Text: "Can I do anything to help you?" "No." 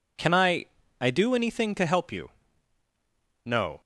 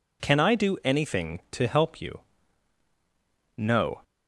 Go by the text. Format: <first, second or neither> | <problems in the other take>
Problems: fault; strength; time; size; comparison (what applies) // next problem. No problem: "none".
second | says "I" twice; at 1.0 s